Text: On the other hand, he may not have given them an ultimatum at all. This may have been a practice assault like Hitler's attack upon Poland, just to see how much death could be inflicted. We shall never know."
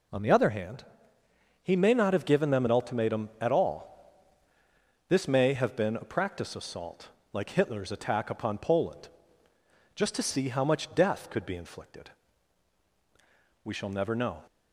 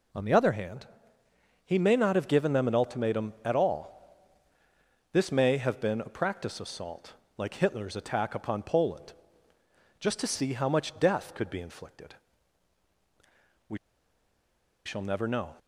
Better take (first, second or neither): first